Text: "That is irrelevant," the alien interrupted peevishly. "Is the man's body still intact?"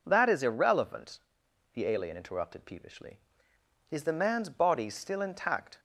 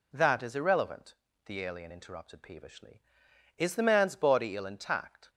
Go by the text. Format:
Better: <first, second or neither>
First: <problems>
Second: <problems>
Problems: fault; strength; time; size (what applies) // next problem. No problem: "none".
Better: first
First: none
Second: says "ill" for "still"; at 4.5 s